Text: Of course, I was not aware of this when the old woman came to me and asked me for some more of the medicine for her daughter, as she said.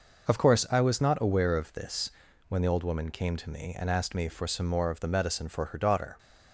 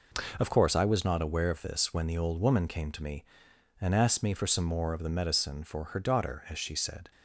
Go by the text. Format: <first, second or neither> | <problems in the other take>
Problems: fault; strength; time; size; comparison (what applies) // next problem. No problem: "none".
second | pauses between "this" and "when"; at 2.0 s; 0.38 s long // stops before "as she said"; at 6.1 s